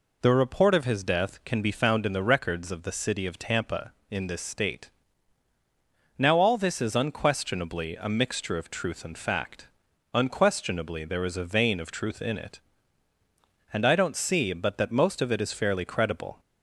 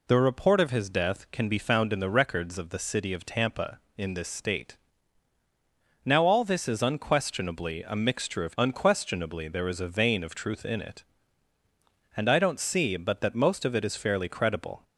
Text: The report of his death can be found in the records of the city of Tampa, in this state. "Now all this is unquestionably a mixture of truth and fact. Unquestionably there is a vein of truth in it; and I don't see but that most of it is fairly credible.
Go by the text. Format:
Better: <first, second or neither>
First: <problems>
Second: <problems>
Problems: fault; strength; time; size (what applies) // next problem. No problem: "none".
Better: first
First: none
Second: skips "truth and fact"; at 8.5 s